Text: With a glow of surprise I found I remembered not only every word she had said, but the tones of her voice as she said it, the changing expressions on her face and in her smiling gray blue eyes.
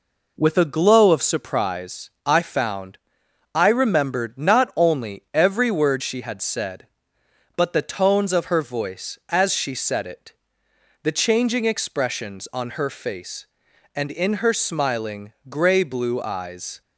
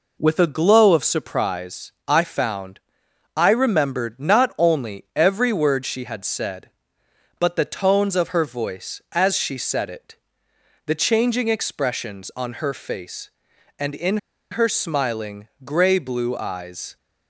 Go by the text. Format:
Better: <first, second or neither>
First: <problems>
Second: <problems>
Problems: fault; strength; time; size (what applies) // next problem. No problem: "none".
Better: first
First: pauses between "found" and "I"; noticeable; at 2.9 s; 0.56 s long // pauses between "smiling" and "gray"; slight; at 15.3 s; 0.16 s long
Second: pauses between "found" and "I"; noticeable; at 2.8 s; 0.56 s long // pauses between "in" and "her"; slight; at 14.1 s; 0.34 s long // pauses between "smiling" and "gray"; slight; at 15.4 s; 0.16 s long